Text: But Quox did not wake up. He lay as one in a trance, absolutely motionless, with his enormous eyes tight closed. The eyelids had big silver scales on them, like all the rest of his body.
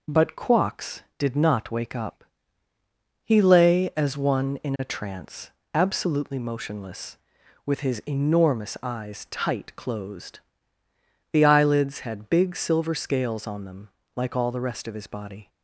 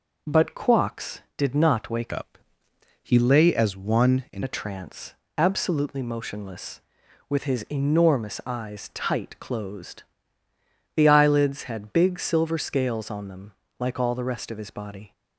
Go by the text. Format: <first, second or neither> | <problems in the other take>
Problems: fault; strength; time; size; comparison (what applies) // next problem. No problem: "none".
first | changes voice from "up" to "in"; from 2.1 to 4.4 s; 2.3 s long